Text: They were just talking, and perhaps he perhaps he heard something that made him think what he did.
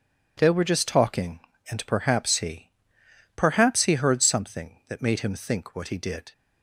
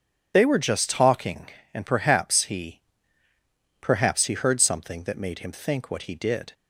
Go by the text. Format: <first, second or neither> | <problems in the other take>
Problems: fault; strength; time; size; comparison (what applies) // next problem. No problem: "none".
first | loses the start of "They"; at 0.3 s; 45 ms // pauses between "he" and "perhaps"; at 2.8 s; 1.0 s long; noticeable in the first